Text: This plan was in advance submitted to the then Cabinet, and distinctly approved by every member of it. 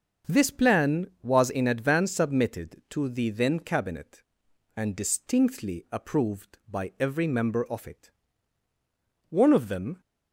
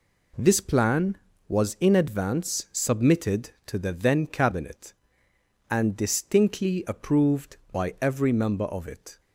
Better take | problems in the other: second | starts louder than the rest; noticeable; until 1.3 s; 6 dB // goes on to say "One of them"; noticeable; from 9.2 s on; 0.72 s long

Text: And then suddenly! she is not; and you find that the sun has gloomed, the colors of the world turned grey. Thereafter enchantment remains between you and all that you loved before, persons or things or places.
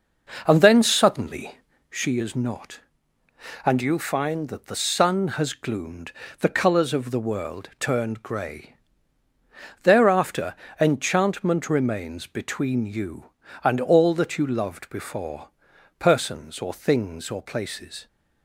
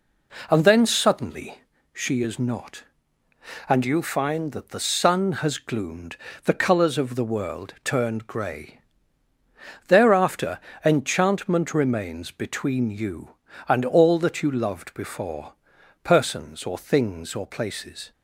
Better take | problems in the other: second | starts louder than the rest; noticeable; until 2.2 s; 5.5 dB // pauses between "Thereafter" and "enchantment"; slight; at 10.5 s; 0.26 s long; slight in the second

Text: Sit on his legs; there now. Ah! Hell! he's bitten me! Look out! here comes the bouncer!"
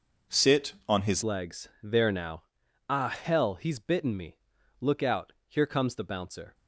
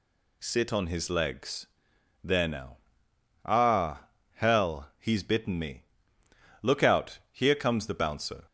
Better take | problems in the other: second | changes voice at "legs"; from 1.2 s on; 5.3 s long

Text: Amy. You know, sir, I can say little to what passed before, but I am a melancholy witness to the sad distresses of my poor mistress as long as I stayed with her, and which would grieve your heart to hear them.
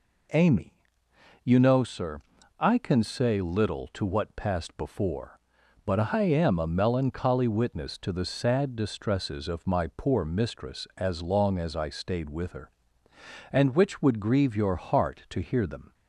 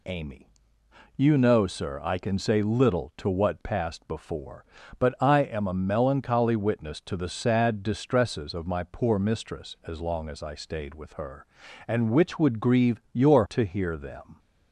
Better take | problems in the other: first | skips "heart"; at 13.4 s

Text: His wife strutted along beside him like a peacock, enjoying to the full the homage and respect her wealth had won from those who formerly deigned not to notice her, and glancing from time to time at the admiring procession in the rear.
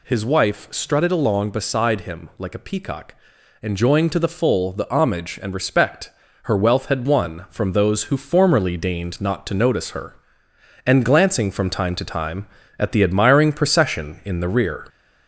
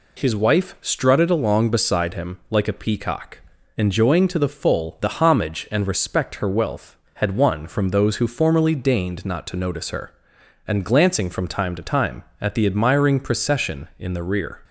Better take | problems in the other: second | gets louder; slight; throughout; 3 dB // pauses between "respect" and "her"; slight; at 6.1 s; 0.32 s long

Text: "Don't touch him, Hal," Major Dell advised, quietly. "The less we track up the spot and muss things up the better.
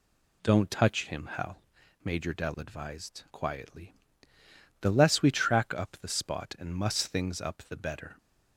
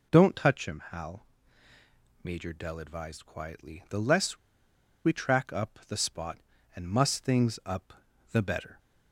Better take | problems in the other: first | pauses between "less" and "we"; noticeable; at 4.3 s; 0.67 s long // pauses between "up" and "the"; at 7.9 s; 0.38 s long

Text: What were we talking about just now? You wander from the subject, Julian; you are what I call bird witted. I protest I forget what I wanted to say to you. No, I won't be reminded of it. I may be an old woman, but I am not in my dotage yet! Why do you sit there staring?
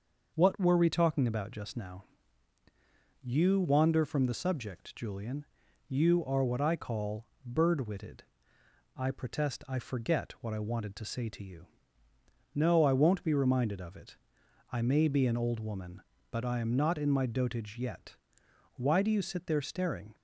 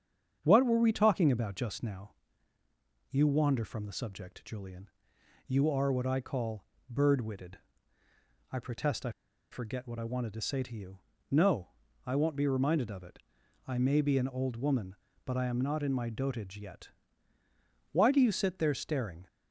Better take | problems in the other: first | starts louder than the rest; strong; until 1.4 s; 8 dB; also in the first // pauses between "call" and "bird"; slight; at 6.6 s; 0.24 s long; slight in the first // pauses between "I" and "forget"; at 9.0 s; 0.41 s long

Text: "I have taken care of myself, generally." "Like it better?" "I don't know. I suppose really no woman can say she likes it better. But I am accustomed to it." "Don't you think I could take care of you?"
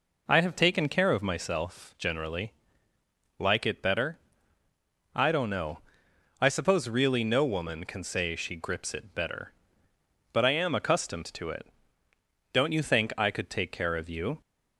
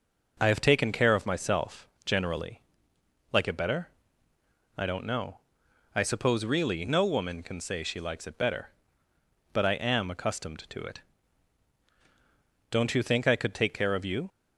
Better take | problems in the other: second | says "grips" for "likes"; at 8.5 s

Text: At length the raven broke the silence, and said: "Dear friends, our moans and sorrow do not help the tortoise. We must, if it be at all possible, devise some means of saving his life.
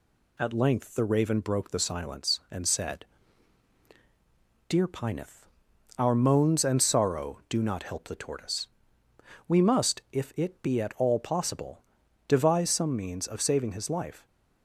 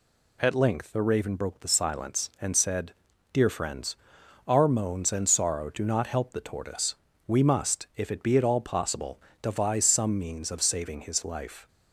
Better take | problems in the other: second | says "pineth" for "friends"; at 4.8 s

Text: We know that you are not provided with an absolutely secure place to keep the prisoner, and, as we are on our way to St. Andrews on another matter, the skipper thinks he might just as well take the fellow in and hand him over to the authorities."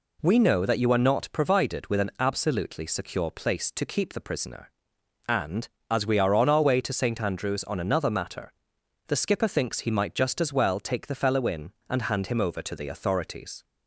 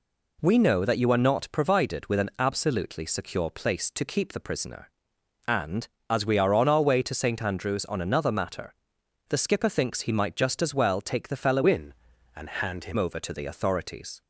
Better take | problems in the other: first | changes voice from "in" to "him"; from 11.6 to 12.9 s; 1.3 s long

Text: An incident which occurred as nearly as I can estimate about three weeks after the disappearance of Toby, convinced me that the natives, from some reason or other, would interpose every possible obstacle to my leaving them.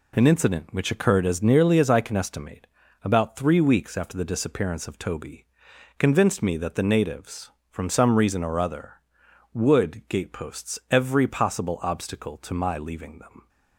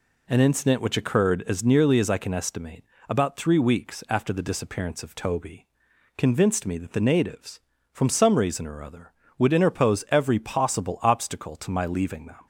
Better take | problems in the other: second | pauses between "estimate" and "about"; slight; at 2.6 s; 0.34 s long; slight in the second // says "gateposts" for "interpose"; at 10.0 s

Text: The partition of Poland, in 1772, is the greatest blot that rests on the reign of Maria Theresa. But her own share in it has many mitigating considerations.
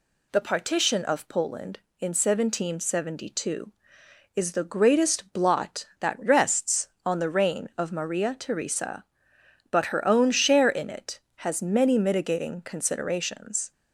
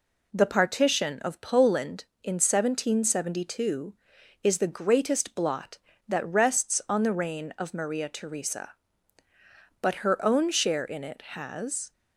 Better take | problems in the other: first | stops before "many mitigating considerations"; at 11.9 s

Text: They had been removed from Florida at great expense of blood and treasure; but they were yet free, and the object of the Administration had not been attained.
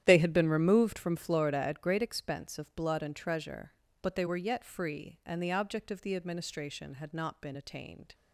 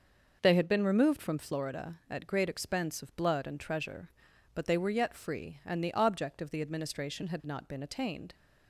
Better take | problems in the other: second | starts louder than the rest; strong; until 1.2 s; 11 dB

